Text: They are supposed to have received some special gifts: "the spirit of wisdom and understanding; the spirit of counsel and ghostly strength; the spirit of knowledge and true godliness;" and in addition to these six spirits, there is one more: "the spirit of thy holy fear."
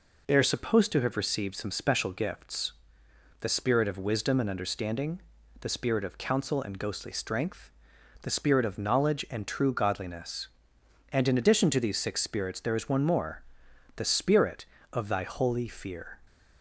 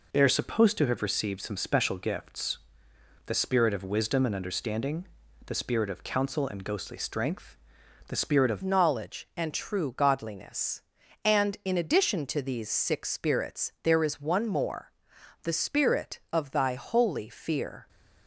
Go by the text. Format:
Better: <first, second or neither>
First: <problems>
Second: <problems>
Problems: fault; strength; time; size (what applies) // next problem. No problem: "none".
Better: first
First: none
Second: changes voice at "knowledge"; from 8.6 s on; 9.2 s long